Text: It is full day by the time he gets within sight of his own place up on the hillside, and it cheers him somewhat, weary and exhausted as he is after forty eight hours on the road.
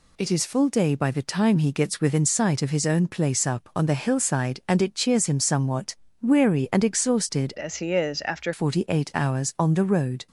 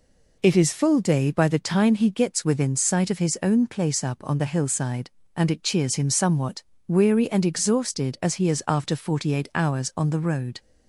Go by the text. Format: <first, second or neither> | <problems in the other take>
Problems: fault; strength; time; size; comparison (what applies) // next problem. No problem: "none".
second | changes voice from "as" to "after"; from 7.5 to 8.5 s; 1.0 s long